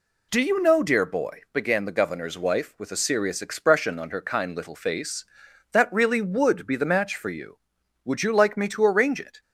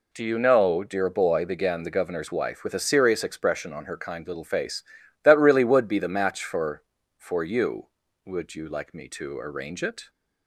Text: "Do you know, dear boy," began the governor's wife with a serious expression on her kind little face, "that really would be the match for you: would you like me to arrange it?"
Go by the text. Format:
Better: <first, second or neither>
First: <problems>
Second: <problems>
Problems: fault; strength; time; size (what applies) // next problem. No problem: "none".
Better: first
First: none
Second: says "for" twice; at 7.1 s